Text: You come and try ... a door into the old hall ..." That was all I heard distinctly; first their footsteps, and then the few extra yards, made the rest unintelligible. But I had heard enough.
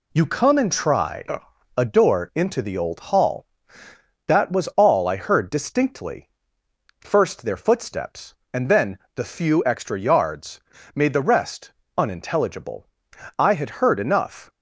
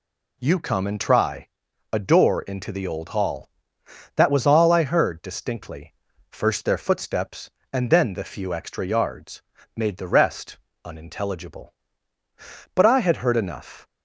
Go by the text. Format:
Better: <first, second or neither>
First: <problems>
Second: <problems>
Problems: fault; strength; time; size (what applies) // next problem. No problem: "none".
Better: second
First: pauses between "then" and "the"; slight; at 8.9 s; 0.16 s long // pauses between "rest" and "unintelligible"; slight; at 11.7 s; 0.26 s long // skips "But"; at 13.1 s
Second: pauses between "rest" and "unintelligible"; slight; at 10.5 s; 0.26 s long